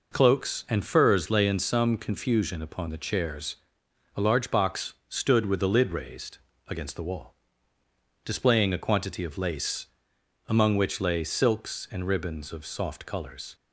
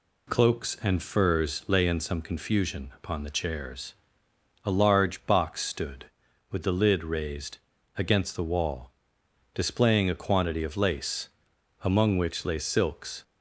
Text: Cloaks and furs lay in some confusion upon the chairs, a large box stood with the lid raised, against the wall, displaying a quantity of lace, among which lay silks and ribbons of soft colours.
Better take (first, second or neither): first